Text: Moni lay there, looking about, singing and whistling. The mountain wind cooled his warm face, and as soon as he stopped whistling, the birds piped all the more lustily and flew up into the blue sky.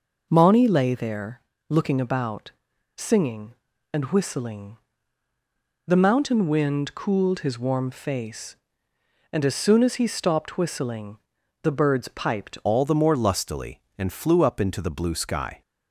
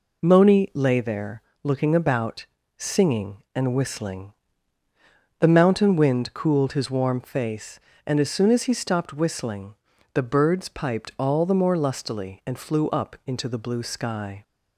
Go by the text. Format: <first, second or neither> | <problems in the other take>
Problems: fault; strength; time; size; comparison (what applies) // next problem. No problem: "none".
second | changes voice at "all"; from 12.6 s on; 3.0 s long